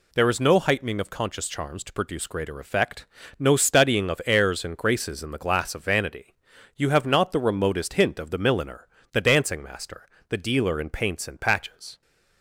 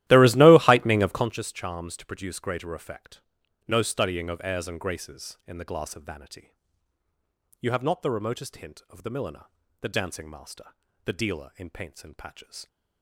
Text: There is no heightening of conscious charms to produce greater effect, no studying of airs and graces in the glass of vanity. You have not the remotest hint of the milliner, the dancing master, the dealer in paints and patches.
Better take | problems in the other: first | starts louder than the rest; strong; until 1.3 s; 14.5 dB

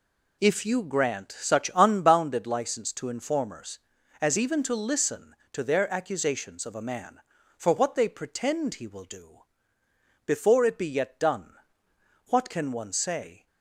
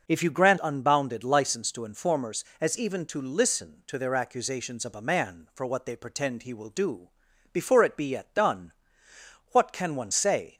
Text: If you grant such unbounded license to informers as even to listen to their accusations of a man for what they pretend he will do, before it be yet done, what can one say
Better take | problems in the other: first | skips "such"; at 0.5 s

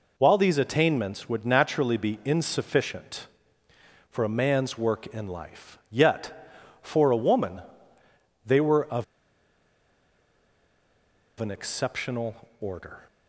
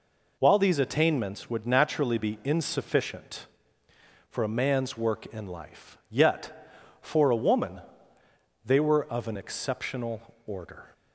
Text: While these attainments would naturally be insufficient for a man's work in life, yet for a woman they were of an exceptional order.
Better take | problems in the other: second | pauses between "woman" and "they"; noticeable; at 7.6 s; 0.82 s long; noticeable in the second // pauses between "of" and "an"; strong; at 9.0 s; 2.3 s long

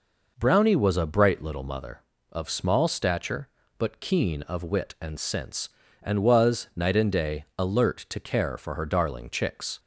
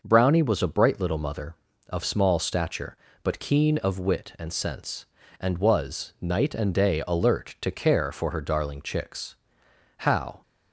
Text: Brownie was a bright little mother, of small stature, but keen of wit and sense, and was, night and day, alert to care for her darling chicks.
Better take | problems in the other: first | goes on to say "How"; slight; from 9.9 s on; 0.44 s long

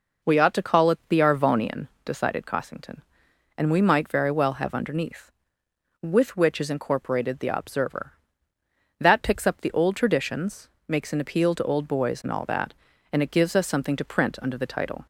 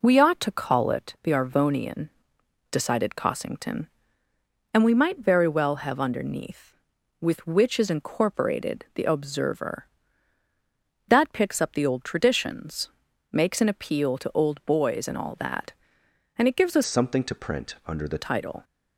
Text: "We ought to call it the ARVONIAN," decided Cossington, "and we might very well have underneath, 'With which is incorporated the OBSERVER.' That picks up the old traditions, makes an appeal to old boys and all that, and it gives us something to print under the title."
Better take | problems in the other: first | changes voice from "something" to "the"; from 16.8 to 18.1 s; 1.3 s long

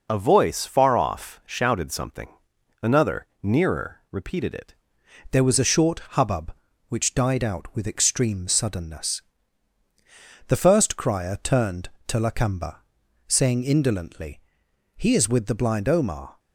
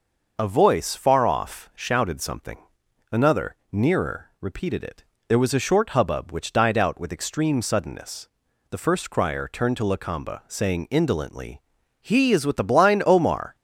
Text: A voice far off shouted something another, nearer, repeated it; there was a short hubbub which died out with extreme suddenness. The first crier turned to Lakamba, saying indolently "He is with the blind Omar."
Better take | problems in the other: second | pauses between "something" and "another"; noticeable; at 2.2 s; 0.52 s long; noticeable in the second // changes voice at "there"; from 5.3 s on; 11.0 s long // pauses between "short" and "hubbub"; slight; at 5.9 s; 0.16 s long // pauses between "indolently" and "He"; noticeable; at 14.4 s; 0.56 s long; also in the second

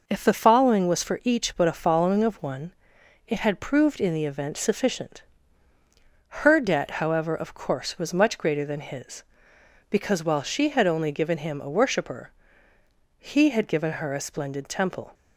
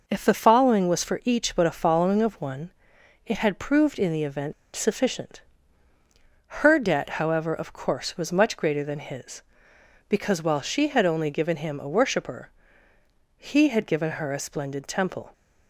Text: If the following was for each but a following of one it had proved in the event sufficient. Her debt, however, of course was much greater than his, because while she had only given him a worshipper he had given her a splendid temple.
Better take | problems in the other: first | pauses between "one" and "it"; noticeable; at 2.7 s; 0.56 s long; noticeable in the first // pauses between "event" and "sufficient"; slight; at 4.5 s; 0.21 s long // pauses between "worshipper" and "he"; noticeable; at 12.4 s; 0.90 s long; noticeable in the first

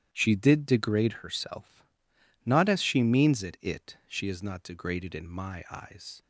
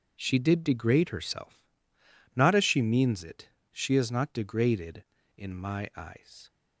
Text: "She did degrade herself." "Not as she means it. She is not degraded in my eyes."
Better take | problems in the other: second | starts louder than the rest; strong; until 1.1 s; 10.5 dB; noticeable in the second // says "it" twice; at 3.6 s

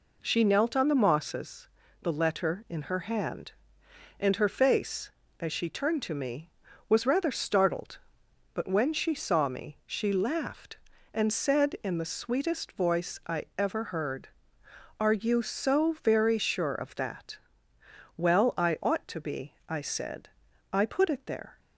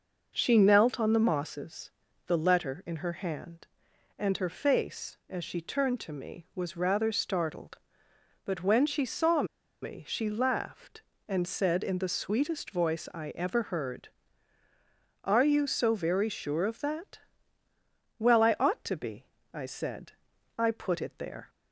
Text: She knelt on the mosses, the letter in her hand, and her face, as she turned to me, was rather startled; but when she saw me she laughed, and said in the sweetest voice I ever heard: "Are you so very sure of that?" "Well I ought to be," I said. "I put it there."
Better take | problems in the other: first | pauses between "saw" and "me"; at 9.4 s; 0.38 s long

